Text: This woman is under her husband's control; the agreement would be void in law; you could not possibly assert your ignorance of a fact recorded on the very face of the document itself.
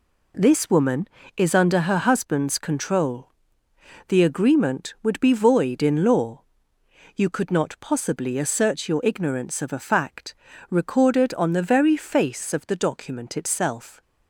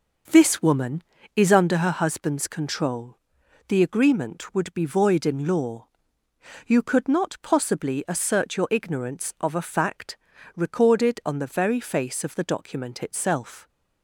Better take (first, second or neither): first